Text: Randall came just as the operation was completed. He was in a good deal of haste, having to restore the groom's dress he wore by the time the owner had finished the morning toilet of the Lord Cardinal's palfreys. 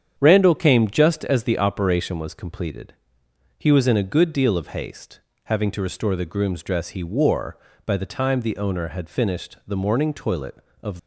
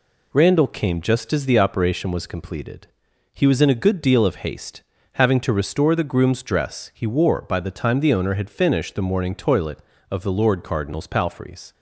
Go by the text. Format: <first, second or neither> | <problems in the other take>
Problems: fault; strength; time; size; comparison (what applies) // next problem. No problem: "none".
second | starts louder than the rest; strong; until 1.1 s; 8 dB // stops before "the Lord Cardinal's palfreys"; at 10.9 s